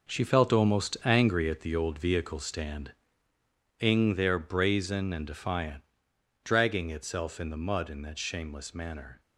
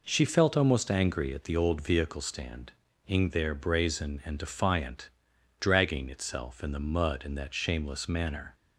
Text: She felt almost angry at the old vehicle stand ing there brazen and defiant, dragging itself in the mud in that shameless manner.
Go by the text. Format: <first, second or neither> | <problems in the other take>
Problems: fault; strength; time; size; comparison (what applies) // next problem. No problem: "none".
second | gets quieter; strong; throughout; 9.5 dB // pauses between "stand" and "ing"; noticeable; at 2.9 s; 0.88 s long; slight in the second